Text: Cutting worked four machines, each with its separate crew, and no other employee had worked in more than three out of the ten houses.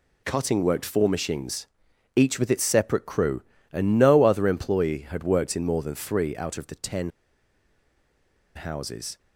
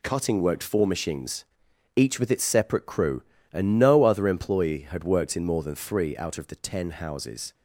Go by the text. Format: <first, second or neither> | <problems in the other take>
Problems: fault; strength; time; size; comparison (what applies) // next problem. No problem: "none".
second | pauses between "ten" and "houses"; strong; at 7.1 s; 1.4 s long